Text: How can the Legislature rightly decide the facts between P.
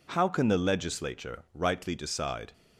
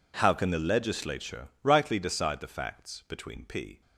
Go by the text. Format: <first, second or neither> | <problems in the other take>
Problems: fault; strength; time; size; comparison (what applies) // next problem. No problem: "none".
second | stops before "the facts between P"; at 2.5 s